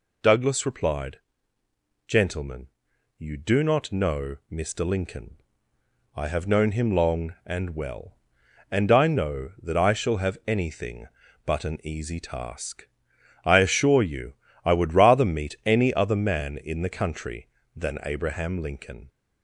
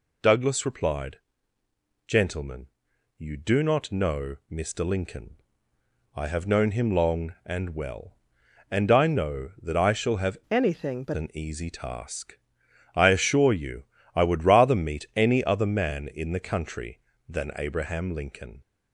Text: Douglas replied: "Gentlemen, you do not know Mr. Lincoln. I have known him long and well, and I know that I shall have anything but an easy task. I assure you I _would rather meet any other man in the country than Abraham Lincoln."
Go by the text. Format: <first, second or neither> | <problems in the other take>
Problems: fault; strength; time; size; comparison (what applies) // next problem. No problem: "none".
first | changes voice from "anything" to "but"; from 10.5 to 11.1 s; 0.6 s long // pauses between "you" and "I"; slight; at 13.8 s; 0.32 s long; slight in the first